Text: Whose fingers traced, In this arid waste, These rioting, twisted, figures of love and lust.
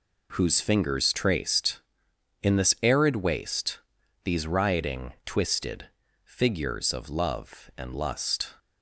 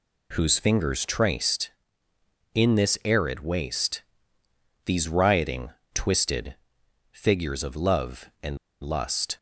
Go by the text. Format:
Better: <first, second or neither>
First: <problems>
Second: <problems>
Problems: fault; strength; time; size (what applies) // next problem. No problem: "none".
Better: first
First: none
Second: pauses between "and" and "lust"; slight; at 8.5 s; 0.23 s long